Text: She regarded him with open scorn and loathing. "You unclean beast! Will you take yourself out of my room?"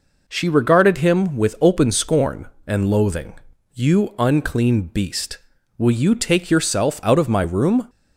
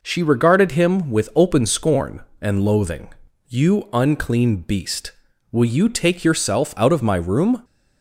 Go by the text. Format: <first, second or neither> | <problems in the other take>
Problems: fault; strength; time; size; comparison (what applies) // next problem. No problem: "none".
neither | none